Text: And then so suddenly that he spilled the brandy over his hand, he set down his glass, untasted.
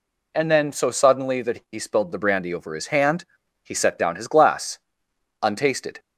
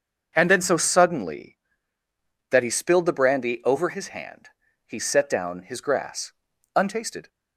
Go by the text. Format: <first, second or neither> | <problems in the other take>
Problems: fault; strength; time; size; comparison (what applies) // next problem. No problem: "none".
first | starts louder than the rest; until 1.3 s; 6.5 dB // says "grass" for "glass"; at 5.7 s